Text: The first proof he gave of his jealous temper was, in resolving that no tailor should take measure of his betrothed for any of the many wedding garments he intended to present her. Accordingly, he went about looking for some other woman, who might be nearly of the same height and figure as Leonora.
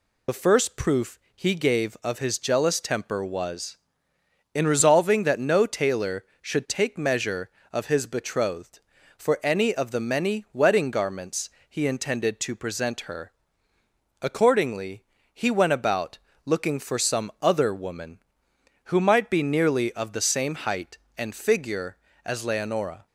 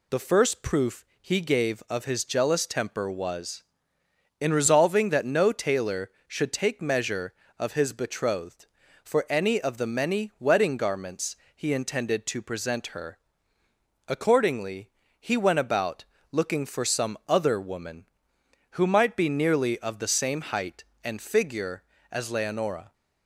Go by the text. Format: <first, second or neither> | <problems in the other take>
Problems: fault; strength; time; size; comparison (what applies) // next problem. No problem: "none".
second | loses the start of "The"; at 0.2 s; 45 ms // pauses between "proof" and "he"; slight; at 1.1 s; 0.16 s long; slight in the second // pauses between "garments" and "he"; slight; at 11.4 s; 0.20 s long; slight in the second // pauses between "about" and "looking"; slight; at 16.1 s; 0.26 s long; slight in the second